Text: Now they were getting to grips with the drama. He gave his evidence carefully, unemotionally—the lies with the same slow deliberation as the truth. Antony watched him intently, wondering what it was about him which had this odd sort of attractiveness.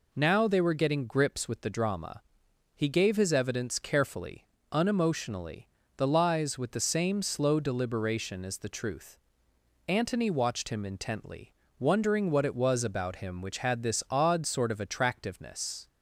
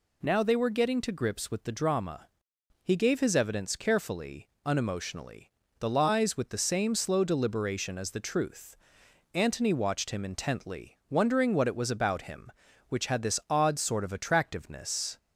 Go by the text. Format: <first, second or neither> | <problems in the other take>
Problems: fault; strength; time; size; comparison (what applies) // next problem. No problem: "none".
second | skips "to"; at 1.0 s